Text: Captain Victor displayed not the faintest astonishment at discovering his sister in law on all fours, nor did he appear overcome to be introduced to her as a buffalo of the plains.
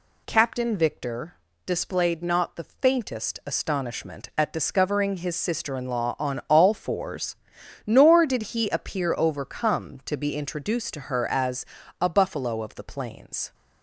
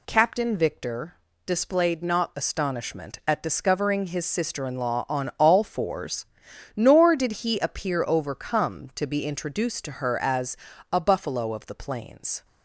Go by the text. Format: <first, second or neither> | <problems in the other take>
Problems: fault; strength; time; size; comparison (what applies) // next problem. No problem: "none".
first | pauses between "Victor" and "displayed"; slight; at 1.1 s; 0.30 s long; slight in the first // skips "the faintest"; at 2.3 s // pauses between "as" and "a"; slight; at 10.5 s; 0.34 s long; slight in the first